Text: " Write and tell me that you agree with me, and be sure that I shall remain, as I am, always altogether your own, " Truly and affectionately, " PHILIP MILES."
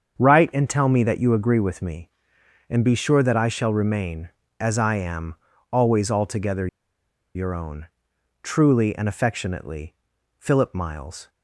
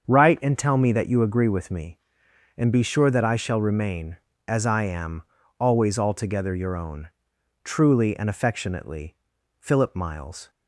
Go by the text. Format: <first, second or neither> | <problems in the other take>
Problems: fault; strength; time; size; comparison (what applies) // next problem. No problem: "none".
second | starts louder than the rest; strong; until 1.1 s; 7 dB; strong in the second // pauses between "altogether" and "your"; noticeable; at 6.6 s; 0.68 s long